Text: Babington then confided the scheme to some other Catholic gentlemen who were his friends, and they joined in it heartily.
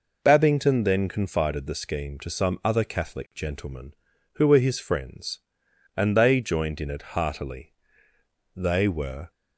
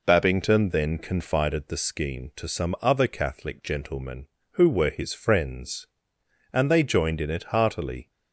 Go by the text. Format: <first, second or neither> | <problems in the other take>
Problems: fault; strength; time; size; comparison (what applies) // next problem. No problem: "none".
second | goes on to say "They were"; noticeable; from 8.5 s on; 0.74 s long